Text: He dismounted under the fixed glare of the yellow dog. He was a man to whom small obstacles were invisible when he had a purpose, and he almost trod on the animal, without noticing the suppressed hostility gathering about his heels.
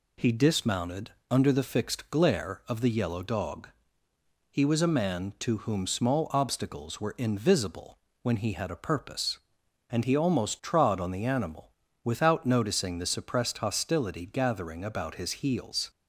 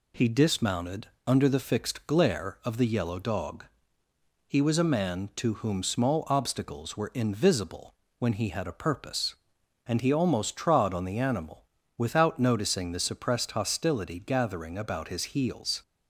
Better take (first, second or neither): neither